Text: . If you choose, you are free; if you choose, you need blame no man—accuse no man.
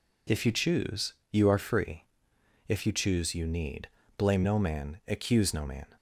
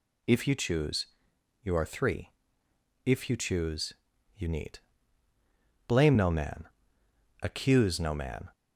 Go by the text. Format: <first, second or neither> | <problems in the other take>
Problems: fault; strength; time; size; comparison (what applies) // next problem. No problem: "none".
first | says "three" for "free"; at 1.8 s // pauses between "need" and "blame"; at 4.7 s; 1.1 s long; slight in the first